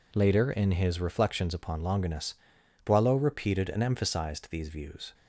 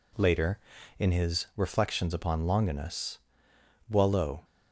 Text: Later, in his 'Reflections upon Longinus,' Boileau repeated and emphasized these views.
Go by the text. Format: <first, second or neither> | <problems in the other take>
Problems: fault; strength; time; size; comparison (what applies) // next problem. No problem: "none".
first | stops before "repeated and emphasized these views"; at 4.4 s